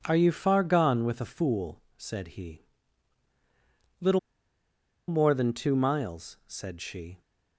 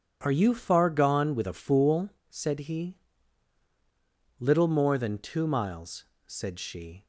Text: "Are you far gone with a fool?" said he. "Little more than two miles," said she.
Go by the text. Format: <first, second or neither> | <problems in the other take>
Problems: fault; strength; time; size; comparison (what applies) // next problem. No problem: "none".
second | pauses between "Little" and "more"; noticeable; at 4.1 s; 0.88 s long